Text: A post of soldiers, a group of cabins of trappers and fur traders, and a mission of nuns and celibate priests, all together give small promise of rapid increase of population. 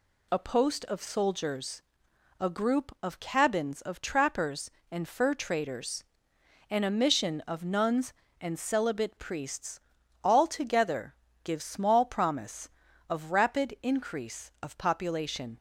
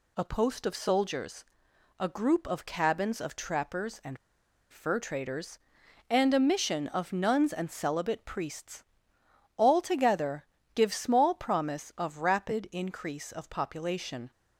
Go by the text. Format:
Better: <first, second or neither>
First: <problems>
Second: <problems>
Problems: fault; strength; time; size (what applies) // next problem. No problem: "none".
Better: first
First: pauses between "together" and "give"; slight; at 11.1 s; 0.28 s long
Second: pauses between "and" and "fur"; noticeable; at 4.1 s; 0.55 s long // pauses between "together" and "give"; slight; at 10.4 s; 0.26 s long